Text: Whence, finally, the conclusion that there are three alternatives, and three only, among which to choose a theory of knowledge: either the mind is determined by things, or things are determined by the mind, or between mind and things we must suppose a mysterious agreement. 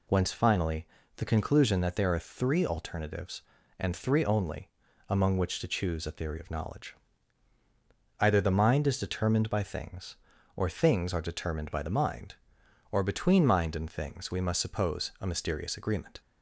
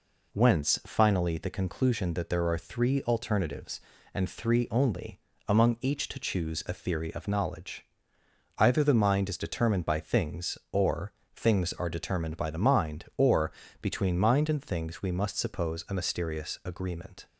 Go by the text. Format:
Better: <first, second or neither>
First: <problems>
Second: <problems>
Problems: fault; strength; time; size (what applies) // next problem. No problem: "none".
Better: first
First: none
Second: says "each" for "which"; at 5.8 s // pauses between "or" and "things"; slight; at 11.1 s; 0.24 s long // pauses between "or" and "between"; slight; at 13.5 s; 0.30 s long